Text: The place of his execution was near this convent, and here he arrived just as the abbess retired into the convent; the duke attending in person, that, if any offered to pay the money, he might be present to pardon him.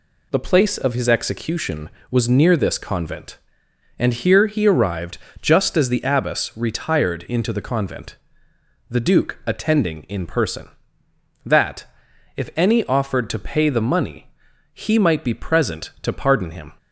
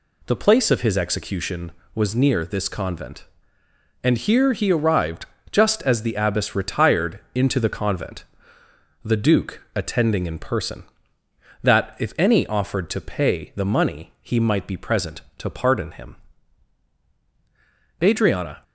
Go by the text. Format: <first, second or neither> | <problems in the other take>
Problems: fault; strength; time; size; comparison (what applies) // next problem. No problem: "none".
first | pauses between "arrived" and "just"; slight; at 5.2 s; 0.26 s long; slight in the first // pauses between "retired" and "into"; slight; at 7.1 s; 0.16 s long // goes on to say "Adriana"; noticeable; from 18.0 s on; 0.62 s long